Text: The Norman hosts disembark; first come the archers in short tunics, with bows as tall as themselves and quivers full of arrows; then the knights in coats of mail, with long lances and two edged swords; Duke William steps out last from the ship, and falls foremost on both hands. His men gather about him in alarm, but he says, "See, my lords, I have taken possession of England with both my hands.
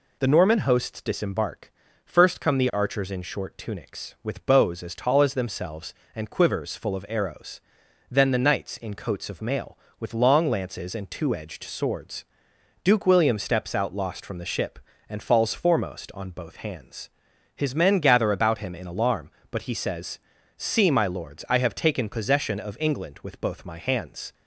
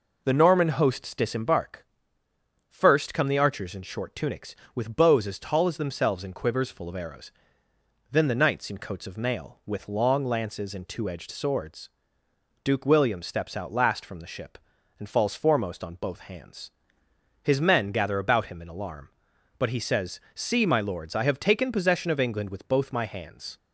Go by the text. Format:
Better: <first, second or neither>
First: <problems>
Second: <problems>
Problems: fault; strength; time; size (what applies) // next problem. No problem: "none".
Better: second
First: says "lost" for "last"; at 13.9 s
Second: none